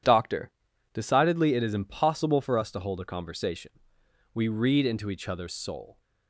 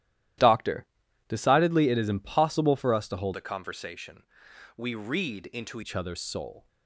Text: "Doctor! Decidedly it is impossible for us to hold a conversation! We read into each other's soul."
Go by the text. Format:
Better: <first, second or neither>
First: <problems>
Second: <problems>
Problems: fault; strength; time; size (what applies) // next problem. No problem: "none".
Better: first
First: none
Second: starts louder than the rest; strong; until 1.8 s; 13.5 dB // changes voice from "a" to "into"; from 3.3 to 5.8 s; 2.5 s long